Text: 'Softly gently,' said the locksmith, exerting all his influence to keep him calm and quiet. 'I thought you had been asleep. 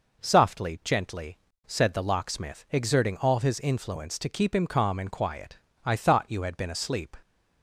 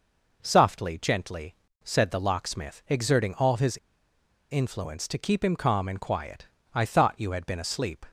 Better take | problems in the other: first | pauses between "his" and "influence"; noticeable; at 3.7 s; 0.75 s long

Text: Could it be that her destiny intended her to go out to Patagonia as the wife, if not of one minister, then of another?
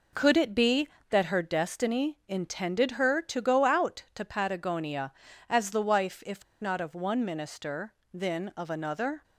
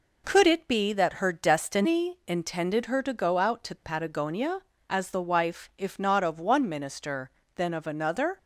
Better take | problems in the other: second | pauses between "if" and "not"; slight; at 6.4 s; 0.17 s long

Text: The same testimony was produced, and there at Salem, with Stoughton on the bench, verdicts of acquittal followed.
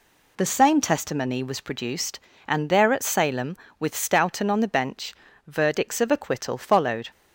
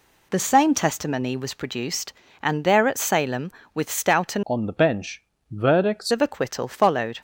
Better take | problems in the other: first | changes voice from "on" to "verdicts"; from 4.4 to 6.1 s; 1.7 s long

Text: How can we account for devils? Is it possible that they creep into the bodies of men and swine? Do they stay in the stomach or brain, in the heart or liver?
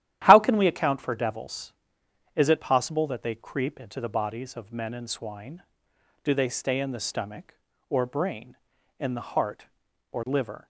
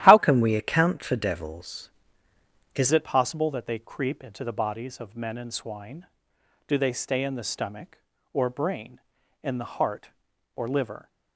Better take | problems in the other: first | starts louder than the rest; strong; until 1.0 s; 12.5 dB; strong in the first // changes voice from "can" to "Is"; from 0.1 to 2.9 s; 2.8 s long

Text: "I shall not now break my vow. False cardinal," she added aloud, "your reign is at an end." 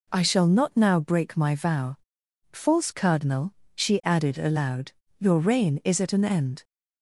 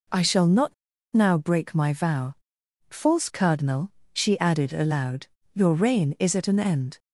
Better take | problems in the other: first | pauses between "not" and "now"; at 0.7 s; 0.38 s long

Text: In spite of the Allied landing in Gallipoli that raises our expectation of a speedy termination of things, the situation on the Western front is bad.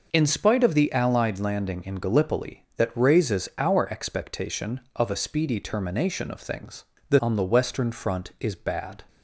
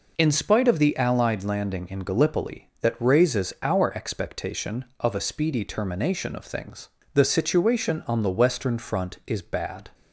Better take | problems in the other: second | skips "situation"; at 7.1 s

